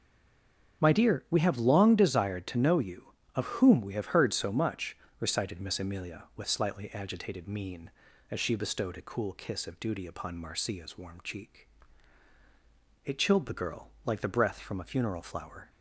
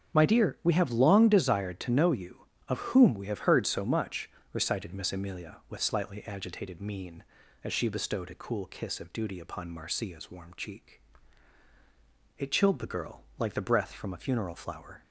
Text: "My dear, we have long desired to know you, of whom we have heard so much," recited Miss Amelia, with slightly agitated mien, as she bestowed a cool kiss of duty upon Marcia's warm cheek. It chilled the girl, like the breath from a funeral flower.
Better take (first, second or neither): second